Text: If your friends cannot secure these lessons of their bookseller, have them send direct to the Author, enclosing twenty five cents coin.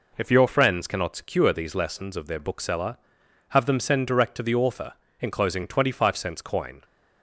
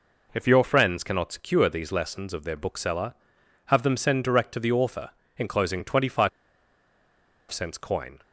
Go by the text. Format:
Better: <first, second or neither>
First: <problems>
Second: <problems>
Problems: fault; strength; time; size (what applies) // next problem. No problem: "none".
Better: first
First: none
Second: pauses between "five" and "cents"; at 6.2 s; 1.2 s long